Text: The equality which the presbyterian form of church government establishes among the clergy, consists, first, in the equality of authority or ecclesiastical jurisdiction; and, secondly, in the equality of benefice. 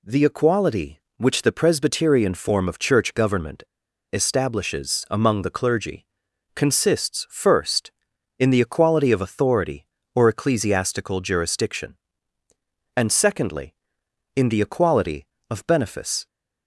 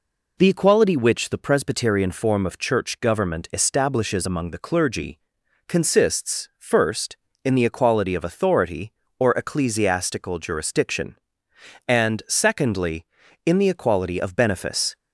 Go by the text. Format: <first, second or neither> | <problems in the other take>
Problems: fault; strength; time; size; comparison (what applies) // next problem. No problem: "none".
second | pauses between "government" and "establishes"; noticeable; at 3.6 s; 0.49 s long